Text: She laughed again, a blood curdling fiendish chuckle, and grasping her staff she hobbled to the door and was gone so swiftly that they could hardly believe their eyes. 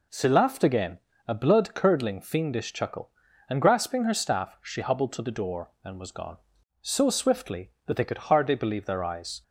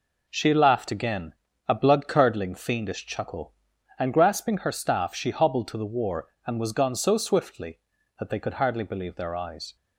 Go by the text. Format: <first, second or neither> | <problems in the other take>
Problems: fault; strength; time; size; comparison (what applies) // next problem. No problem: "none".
first | says "war" for "door"; at 5.8 s